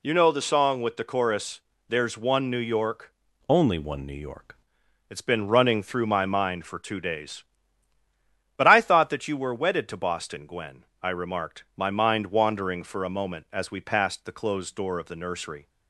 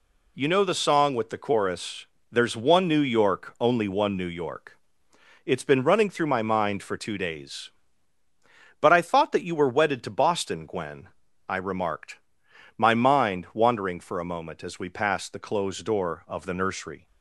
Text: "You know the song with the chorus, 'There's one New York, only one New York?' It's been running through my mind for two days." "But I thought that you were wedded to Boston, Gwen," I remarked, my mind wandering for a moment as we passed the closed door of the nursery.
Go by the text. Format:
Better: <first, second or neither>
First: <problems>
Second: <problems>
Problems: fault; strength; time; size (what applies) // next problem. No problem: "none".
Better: second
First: changes voice from "only" to "York"; from 3.4 to 4.5 s; 1.1 s long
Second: none